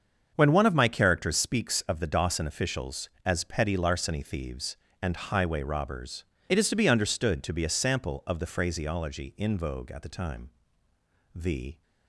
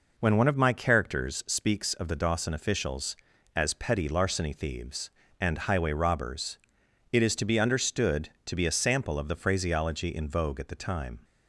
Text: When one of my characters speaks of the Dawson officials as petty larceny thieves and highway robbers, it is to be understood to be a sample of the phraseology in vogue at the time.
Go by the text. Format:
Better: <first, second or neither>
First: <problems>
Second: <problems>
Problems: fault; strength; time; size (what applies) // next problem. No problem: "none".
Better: second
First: starts louder than the rest; until 1.3 s; 7 dB // goes on to say "The"; slight; from 11.3 s on; 0.46 s long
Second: none